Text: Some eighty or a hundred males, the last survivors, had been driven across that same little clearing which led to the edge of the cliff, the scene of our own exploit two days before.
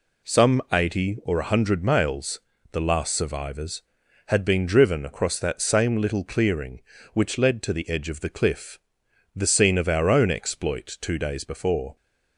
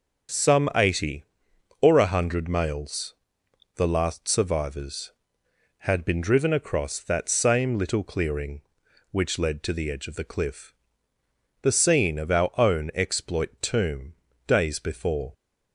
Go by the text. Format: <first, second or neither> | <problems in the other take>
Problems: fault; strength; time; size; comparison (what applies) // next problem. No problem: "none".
first | starts louder than the rest; until 1.9 s; 7 dB // says "tomb" for "two"; at 13.6 s